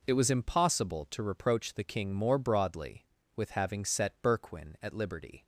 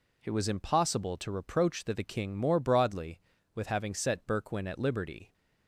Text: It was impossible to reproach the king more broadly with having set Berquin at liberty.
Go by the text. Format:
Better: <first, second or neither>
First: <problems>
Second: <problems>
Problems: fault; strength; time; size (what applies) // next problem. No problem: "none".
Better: first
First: none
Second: says "the" twice; at 1.9 s